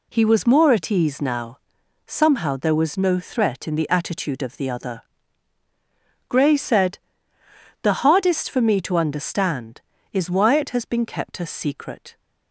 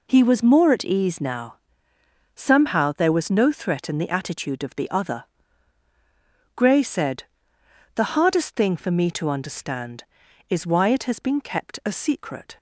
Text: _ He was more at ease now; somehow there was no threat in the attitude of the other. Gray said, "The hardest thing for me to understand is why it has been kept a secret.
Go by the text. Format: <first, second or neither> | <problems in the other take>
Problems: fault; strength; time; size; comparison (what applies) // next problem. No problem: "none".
second | skips "thing"; at 8.4 s